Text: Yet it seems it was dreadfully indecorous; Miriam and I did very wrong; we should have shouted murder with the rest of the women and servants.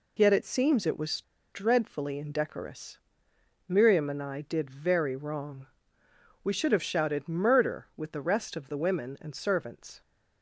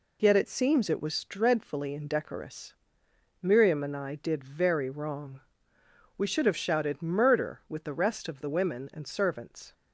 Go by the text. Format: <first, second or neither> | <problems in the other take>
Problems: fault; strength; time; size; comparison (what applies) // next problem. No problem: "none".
second | pauses between "was" and "dreadfully"; slight; at 1.2 s; 0.30 s long